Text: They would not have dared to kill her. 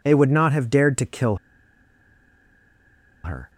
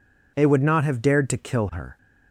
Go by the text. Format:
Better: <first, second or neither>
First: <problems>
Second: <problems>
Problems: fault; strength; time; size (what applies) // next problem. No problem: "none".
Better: second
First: pauses between "kill" and "her"; strong; at 1.3 s; 1.8 s long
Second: none